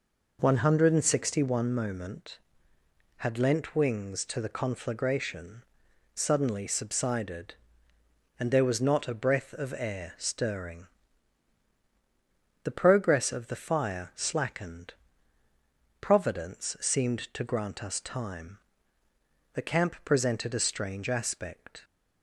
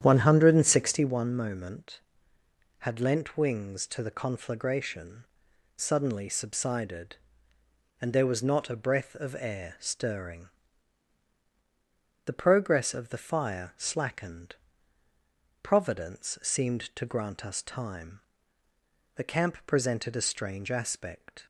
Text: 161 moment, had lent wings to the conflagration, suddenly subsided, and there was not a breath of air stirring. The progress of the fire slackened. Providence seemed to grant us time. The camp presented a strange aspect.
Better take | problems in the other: first | starts louder than the rest; strong; until 1.1 s; 9.5 dB

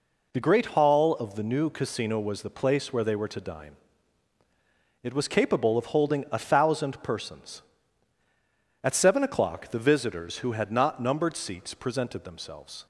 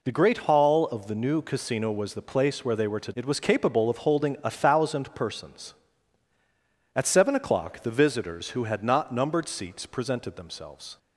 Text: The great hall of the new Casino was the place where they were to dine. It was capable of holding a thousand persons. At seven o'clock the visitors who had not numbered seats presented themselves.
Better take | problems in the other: first | skips "dine"; at 3.1 s

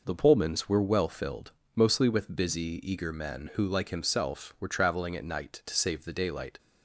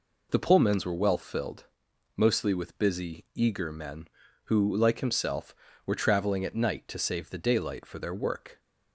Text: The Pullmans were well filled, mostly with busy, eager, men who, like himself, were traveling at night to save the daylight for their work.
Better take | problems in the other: second | stops before "for their work"; at 6.5 s

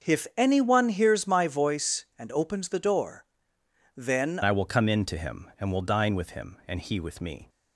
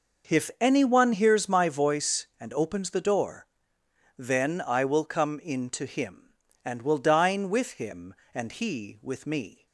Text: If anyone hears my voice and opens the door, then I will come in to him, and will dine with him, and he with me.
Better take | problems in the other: second | starts louder than the rest; until 1.1 s; 6.5 dB // changes voice at "I"; from 4.4 s on; 3.0 s long

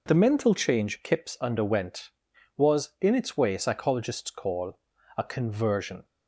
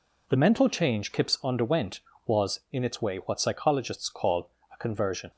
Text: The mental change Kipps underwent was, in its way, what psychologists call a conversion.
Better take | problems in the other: second | skips "what"; at 3.5 s // pauses between "call" and "a"; at 4.7 s; 0.38 s long; slight in the second

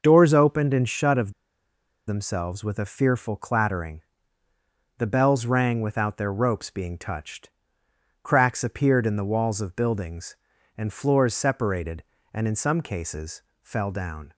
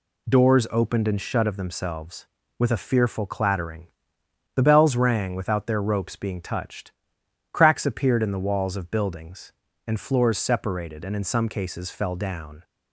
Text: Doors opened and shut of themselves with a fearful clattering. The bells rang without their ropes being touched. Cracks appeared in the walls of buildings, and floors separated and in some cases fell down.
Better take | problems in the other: second | starts louder than the rest; noticeable; until 1.0 s; 6 dB // pauses between "of" and "themselves"; noticeable; at 1.3 s; 0.76 s long // pauses between "cases" and "fell"; slight; at 13.4 s; 0.20 s long

